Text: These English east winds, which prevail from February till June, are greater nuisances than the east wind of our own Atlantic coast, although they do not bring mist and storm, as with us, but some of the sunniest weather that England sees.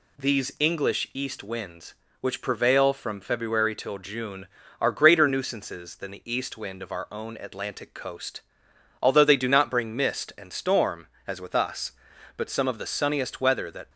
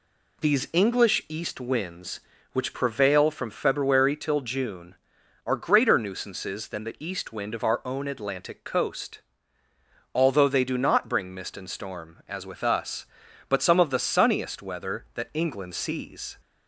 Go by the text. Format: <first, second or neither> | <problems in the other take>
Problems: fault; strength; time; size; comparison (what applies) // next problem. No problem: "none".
second | stops before "England sees"; at 13.8 s